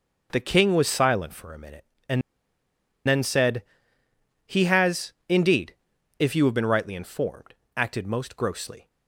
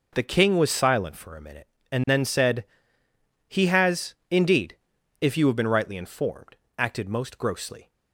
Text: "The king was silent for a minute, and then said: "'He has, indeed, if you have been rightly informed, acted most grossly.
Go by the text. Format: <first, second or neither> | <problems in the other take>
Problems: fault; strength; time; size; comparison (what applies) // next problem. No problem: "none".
second | pauses between "and" and "then"; noticeable; at 2.2 s; 0.86 s long